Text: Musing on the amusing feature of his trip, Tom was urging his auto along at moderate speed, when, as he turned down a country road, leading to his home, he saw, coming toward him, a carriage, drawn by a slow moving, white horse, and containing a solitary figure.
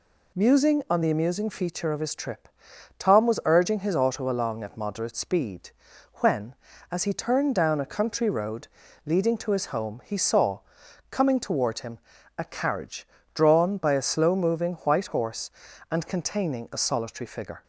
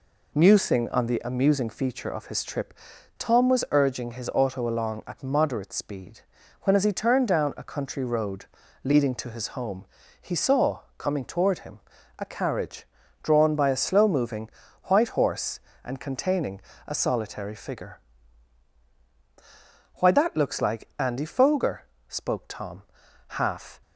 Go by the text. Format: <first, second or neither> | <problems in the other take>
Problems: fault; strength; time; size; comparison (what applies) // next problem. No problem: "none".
first | pauses between "containing" and "a"; slight; at 16.5 s; 0.28 s long // goes on to say "Why that looks like Andy Foger spoke Tom half"; strong; from 19.9 s on; 3.8 s long